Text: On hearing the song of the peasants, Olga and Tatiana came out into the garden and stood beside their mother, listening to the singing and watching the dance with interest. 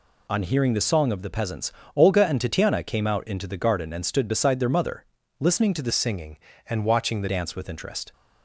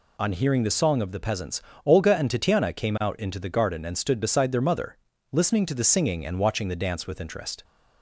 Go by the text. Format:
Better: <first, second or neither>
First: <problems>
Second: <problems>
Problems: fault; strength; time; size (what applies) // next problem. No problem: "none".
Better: second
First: changes voice from "singing" to "the"; from 5.9 to 7.2 s; 1.3 s long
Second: none